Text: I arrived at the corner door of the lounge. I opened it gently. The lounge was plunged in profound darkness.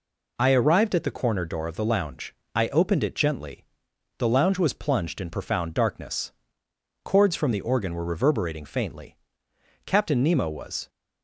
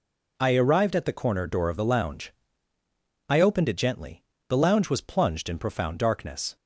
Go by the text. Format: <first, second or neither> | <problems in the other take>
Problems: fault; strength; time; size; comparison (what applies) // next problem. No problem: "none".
second | goes on to say "Chords from the organ were reverberating faintly Captain Nemo was"; strong; from 7.0 s on; 3.8 s long